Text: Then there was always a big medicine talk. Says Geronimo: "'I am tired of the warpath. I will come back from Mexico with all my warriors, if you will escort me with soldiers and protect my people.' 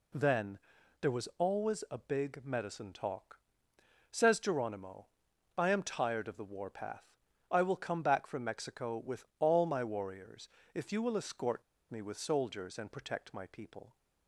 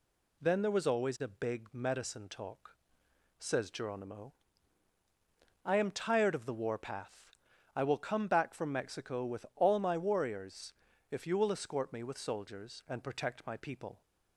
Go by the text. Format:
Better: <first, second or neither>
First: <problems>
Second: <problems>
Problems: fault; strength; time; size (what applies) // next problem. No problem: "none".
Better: second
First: pauses between "Then" and "there"; at 0.5 s; 0.42 s long // pauses between "with" and "all"; slight; at 9.2 s; 0.16 s long // pauses between "escort" and "me"; slight; at 11.6 s; 0.29 s long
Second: none